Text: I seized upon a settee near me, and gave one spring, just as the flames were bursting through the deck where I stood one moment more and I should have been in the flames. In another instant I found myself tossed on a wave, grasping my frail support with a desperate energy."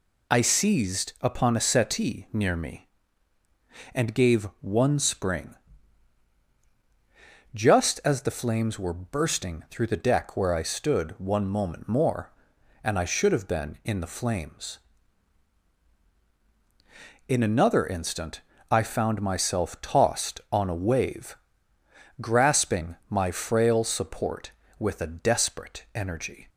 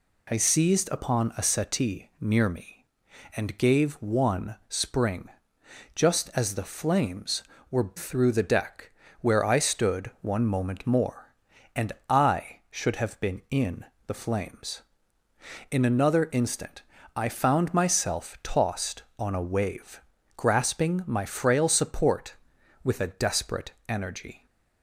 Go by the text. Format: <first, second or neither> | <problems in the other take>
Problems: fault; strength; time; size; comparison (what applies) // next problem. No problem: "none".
first | skips "bursting"; at 7.9 s // pauses between "deck" and "where"; slight; at 8.9 s; 0.30 s long // pauses between "and" and "I"; slight; at 11.9 s; 0.16 s long // pauses between "in" and "the"; slight; at 13.8 s; 0.22 s long // pauses between "instant" and "I"; slight; at 16.8 s; 0.34 s long; slight in the first // pauses between "desperate" and "energy"; slight; at 23.7 s; 0.16 s long